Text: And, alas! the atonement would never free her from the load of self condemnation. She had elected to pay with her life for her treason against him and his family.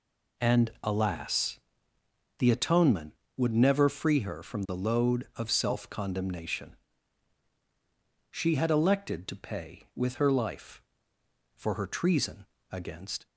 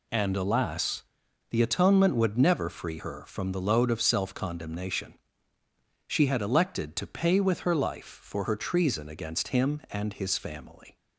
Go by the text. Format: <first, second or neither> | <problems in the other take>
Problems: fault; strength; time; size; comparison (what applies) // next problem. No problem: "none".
second | pauses between "treason" and "against"; slight; at 12.4 s; 0.26 s long // stops before "him and his family"; at 13.2 s